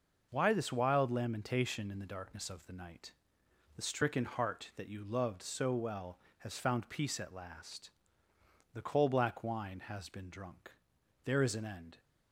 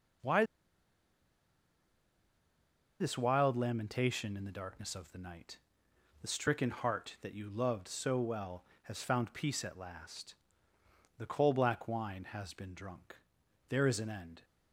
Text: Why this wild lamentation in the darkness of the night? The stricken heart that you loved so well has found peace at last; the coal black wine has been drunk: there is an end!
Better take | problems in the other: first | pauses between "Why" and "this"; strong; at 0.4 s; 2.5 s long

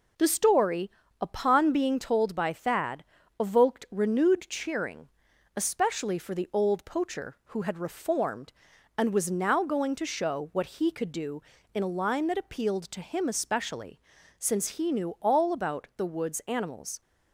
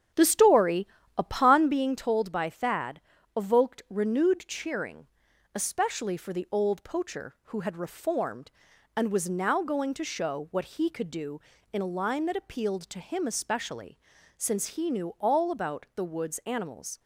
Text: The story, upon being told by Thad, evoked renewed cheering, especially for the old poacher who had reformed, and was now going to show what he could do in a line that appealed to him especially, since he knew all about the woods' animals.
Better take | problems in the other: first | starts louder than the rest; strong; until 1.7 s; 8.5 dB

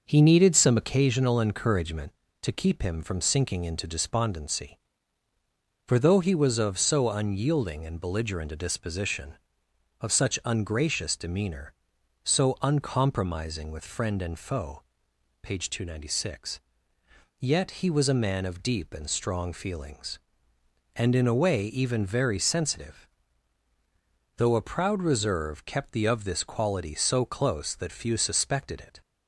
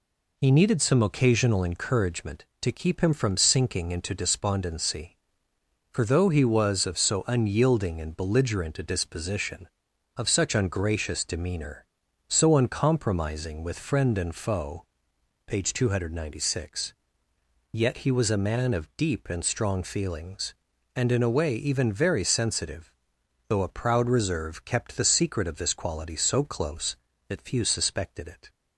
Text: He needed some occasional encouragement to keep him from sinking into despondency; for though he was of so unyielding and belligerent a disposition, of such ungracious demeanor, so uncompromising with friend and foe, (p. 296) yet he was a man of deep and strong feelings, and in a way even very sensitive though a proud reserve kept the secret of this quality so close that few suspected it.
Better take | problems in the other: second | starts louder than the rest; noticeable; until 1.0 s; 6 dB // pauses between "sensitive" and "though"; strong; at 23.0 s; 1.2 s long; noticeable in the second // skips "secret"; at 26.0 s

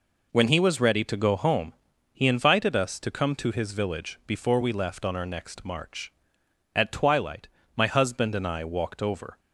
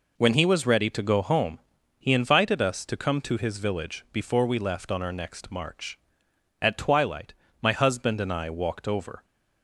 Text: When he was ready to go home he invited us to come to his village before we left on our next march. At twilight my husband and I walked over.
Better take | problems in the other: neither | pauses between "home" and "he"; the same in both // pauses between "twilight" and "my"; slight; the same in both

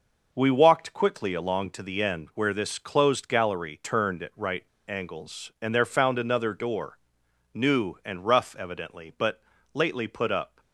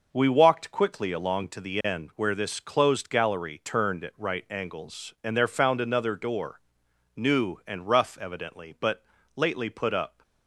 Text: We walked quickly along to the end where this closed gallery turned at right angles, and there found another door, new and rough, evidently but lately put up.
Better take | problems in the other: second | pauses between "right" and "angles"; slight; at 4.6 s; 0.25 s long // pauses between "but" and "lately"; slight; at 9.3 s; 0.34 s long; slight in the second

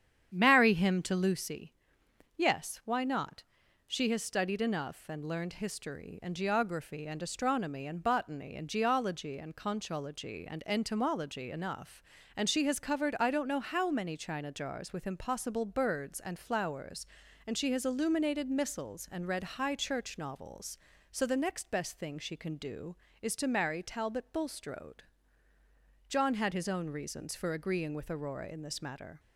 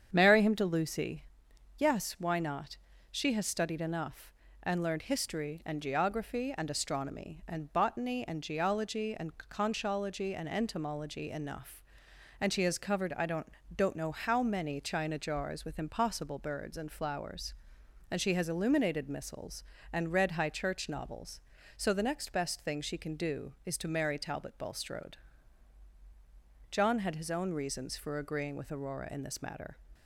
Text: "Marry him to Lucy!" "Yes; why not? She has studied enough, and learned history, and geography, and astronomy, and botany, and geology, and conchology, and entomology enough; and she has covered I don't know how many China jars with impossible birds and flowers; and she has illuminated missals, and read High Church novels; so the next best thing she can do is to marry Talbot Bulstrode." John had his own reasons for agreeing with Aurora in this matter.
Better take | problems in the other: first | starts louder than the rest; strong; until 1.1 s; 8 dB; strong in the first // says "don't" twice; at 13.7 s

